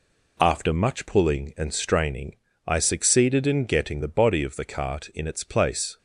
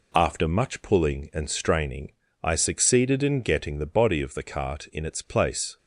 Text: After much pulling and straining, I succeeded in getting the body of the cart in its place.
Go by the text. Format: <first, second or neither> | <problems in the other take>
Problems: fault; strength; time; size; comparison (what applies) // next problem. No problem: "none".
neither | none